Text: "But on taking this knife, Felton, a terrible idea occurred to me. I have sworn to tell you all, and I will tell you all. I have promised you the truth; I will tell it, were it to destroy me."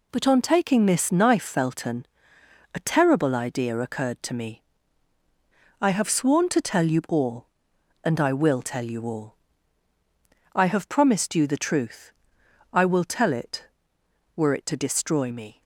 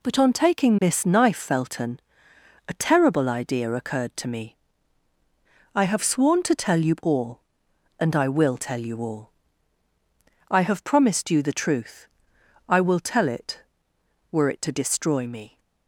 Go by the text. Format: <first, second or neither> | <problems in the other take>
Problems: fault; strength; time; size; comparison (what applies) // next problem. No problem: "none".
neither | none